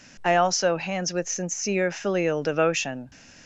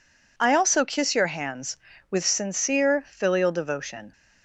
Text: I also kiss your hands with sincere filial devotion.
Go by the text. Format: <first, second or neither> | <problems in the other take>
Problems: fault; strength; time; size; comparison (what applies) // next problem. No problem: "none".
second | skips "kiss your"; at 0.7 s